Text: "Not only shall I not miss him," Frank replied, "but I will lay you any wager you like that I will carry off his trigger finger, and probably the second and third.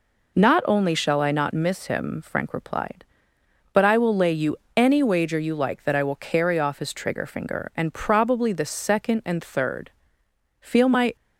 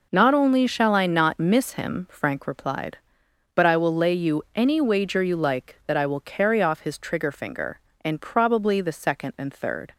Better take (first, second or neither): second